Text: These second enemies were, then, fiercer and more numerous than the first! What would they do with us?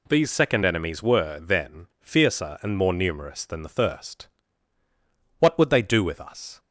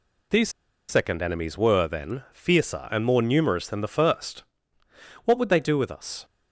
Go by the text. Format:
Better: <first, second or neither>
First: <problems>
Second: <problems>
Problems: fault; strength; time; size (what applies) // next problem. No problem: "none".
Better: first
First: none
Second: pauses between "These" and "second"; at 0.4 s; 0.38 s long